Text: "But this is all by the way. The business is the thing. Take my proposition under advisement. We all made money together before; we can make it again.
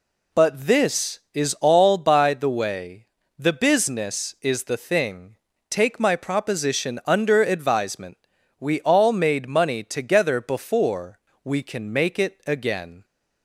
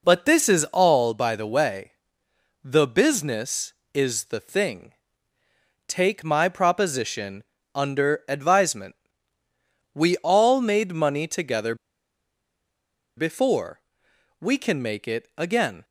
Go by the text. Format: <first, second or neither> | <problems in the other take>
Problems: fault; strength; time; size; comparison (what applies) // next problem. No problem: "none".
first | pauses between "proposition" and "under"; slight; at 7.4 s; 0.32 s long // pauses between "together" and "before"; strong; at 11.7 s; 1.4 s long